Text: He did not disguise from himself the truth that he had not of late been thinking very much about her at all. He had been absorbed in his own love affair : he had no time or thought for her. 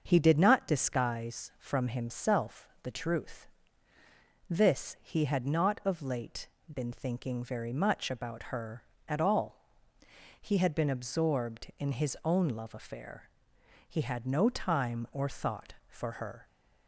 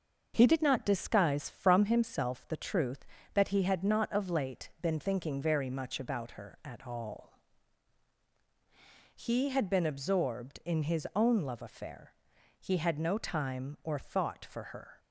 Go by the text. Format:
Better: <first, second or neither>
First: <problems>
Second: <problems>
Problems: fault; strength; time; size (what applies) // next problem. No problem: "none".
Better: second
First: starts louder than the rest; until 1.0 s; 6.5 dB // pauses between "himself" and "the"; slight; at 2.6 s; 0.16 s long // says "this" for "that"; at 4.4 s // pauses between "late" and "been"; slight; at 6.4 s; 0.26 s long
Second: starts louder than the rest; noticeable; until 1.3 s; 6 dB